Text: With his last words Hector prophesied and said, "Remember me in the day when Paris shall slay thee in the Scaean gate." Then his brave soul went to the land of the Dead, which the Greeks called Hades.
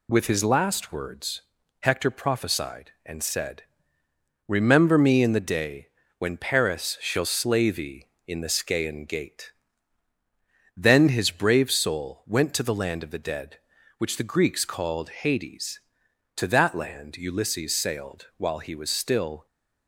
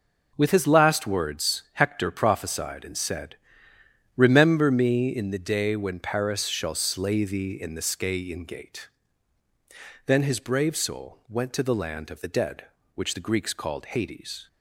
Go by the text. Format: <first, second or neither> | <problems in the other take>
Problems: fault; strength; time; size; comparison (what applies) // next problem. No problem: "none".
second | pauses between "words" and "Hector"; at 1.4 s; 0.40 s long // pauses between "day" and "when"; slight; at 5.8 s; 0.32 s long // goes on to say "To that land Ulysses sailed while he was still"; strong; from 16.3 s on; 3.0 s long